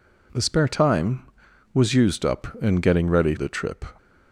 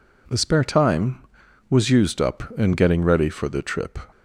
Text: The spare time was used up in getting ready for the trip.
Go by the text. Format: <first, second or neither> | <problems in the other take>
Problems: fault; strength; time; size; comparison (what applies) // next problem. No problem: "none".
second | skips "for"; at 3.3 s